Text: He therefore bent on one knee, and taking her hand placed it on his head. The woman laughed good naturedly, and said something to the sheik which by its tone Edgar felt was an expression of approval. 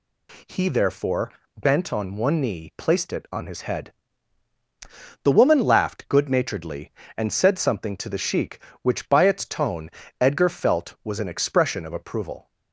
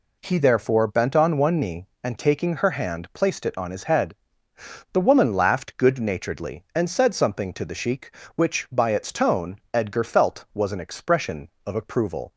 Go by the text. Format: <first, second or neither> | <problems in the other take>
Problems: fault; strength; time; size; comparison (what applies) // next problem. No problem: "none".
second | pauses between "therefore" and "bent"; slight; at 1.3 s; 0.28 s long // skips "and taking her hand"; at 2.7 s // pauses between "tone" and "Edgar"; slight; at 9.9 s; 0.28 s long; slight in the second